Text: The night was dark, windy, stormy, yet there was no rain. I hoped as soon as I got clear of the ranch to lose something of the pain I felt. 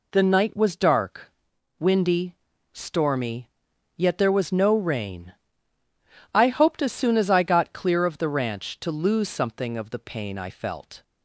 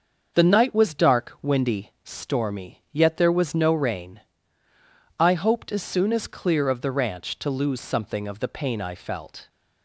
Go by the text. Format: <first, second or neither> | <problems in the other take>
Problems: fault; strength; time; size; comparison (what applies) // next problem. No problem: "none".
first | starts louder than the rest; until 1.3 s; 6.5 dB // skips "I got"; at 6.2 s